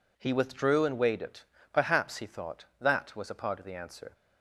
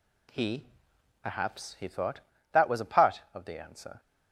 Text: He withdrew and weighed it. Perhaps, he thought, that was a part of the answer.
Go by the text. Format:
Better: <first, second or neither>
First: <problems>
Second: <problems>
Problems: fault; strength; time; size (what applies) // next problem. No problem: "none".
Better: first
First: none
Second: skips "withdrew and weighed it"; at 0.9 s